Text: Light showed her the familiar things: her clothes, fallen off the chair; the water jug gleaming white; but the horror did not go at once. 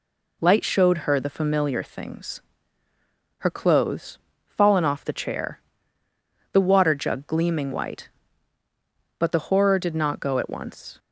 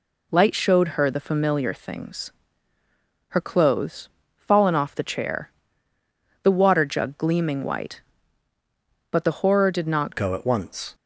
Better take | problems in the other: first | changes voice at "go"; from 10.1 s on; 0.8 s long

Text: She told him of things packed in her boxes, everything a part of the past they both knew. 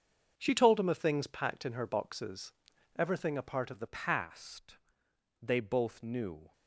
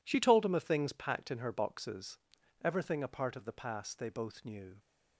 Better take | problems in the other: second | starts louder than the rest; until 1.3 s; 7 dB // changes voice at "past"; from 3.8 s on; 2.7 s long // pauses between "past" and "they"; noticeable; at 4.7 s; 0.64 s long

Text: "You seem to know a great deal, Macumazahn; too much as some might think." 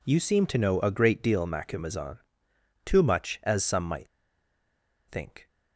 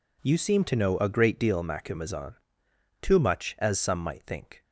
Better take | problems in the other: second | pauses between "might" and "think"; at 4.0 s; 1.0 s long

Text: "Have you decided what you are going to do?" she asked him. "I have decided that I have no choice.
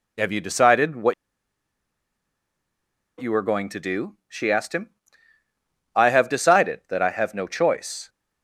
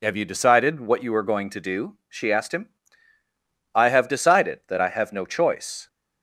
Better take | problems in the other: second | pauses between "what" and "you"; strong; at 1.1 s; 2.0 s long

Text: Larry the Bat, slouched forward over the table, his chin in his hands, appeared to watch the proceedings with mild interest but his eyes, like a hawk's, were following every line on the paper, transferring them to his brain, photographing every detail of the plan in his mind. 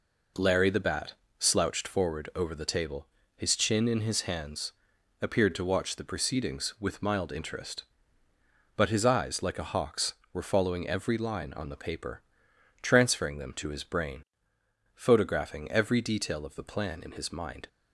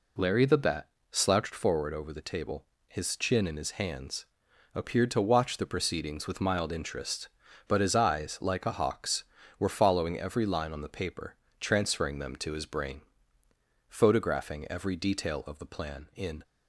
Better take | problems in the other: first | stops before "his mind"; at 16.4 s

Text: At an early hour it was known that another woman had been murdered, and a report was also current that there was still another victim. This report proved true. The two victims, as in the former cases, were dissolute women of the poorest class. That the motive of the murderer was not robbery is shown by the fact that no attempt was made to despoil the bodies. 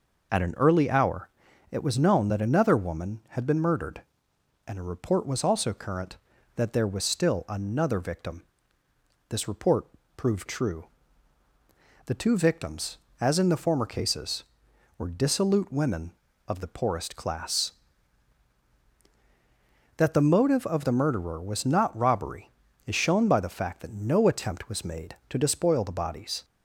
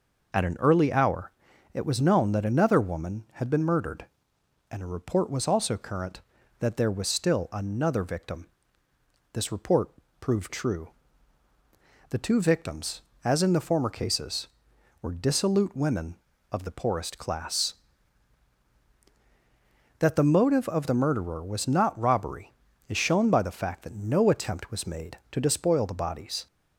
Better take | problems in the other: neither | pauses between "hour" and "it"; the same in both // pauses between "report" and "proved"; slight; the same in both

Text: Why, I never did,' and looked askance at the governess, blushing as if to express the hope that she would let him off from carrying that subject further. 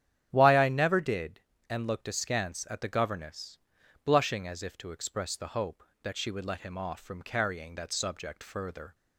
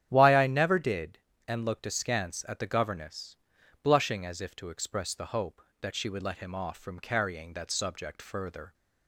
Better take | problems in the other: neither | starts louder than the rest; strong; the same in both

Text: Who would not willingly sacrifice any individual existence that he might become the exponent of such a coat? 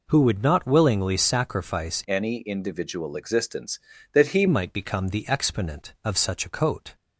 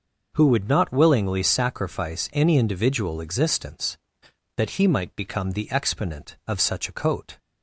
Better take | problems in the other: second | changes voice from "any" to "he"; from 2.0 to 4.4 s; 2.4 s long

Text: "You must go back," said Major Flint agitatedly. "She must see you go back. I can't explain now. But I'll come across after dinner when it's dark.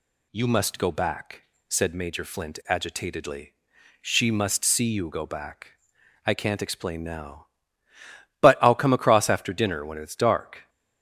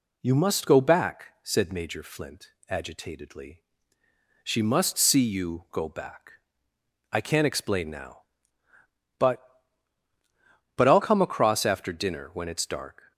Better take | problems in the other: first | pauses between "Flint" and "agitatedly"; slight; at 2.5 s; 0.18 s long // says "But" twice; at 10.7 s

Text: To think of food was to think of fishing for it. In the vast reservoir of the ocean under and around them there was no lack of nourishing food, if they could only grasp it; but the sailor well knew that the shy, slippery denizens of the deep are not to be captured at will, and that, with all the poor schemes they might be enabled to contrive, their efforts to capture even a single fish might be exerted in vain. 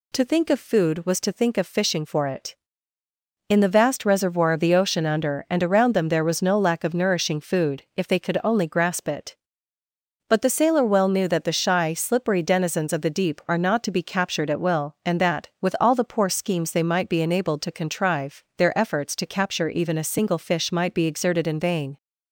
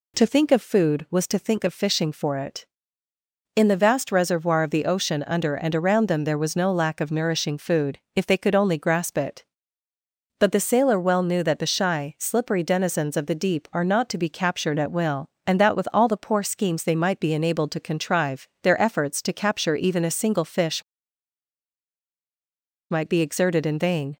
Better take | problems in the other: first | pauses between "fish" and "might"; strong; at 20.8 s; 2.0 s long

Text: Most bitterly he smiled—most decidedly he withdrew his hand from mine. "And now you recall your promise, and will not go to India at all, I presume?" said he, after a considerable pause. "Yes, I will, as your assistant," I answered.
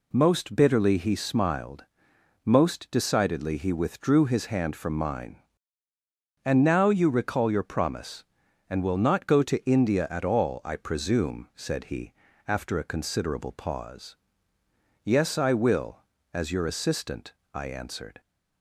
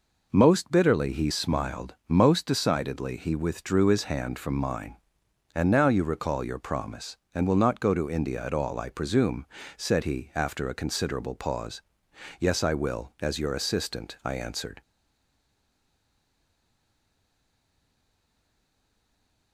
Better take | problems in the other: first | stays silent after the last word; strong; from 14.8 s on; 4.7 s long

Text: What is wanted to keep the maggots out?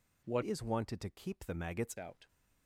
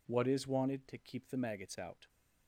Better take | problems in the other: second | changes voice from "is" to "maggots"; from 0.4 to 1.9 s; 1.5 s long

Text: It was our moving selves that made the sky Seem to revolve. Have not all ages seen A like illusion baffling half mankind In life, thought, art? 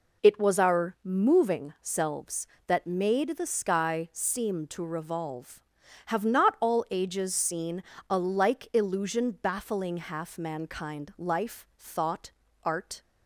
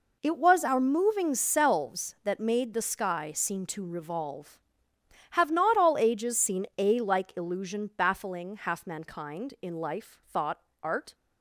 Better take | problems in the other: second | pauses between "seen" and "A"; slight; at 7.8 s; 0.28 s long // skips "In"; at 11.1 s

